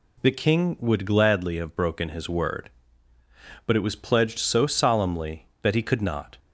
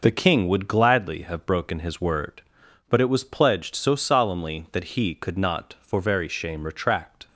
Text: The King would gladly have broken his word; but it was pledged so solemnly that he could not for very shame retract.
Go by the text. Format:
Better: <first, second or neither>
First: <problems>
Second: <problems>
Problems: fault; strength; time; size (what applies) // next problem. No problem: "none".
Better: second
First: stops before "for very shame retract"; at 6.3 s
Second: none